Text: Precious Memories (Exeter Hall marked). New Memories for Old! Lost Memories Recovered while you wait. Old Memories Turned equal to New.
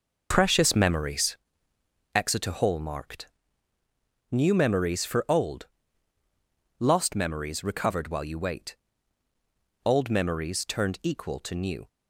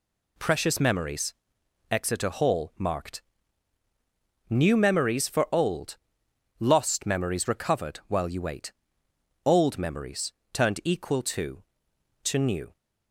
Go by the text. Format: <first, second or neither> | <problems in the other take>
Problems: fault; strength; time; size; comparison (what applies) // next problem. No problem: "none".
first | pauses between "Memories" and "Turned"; slight; at 10.3 s; 0.20 s long // says "to" twice; at 12.2 s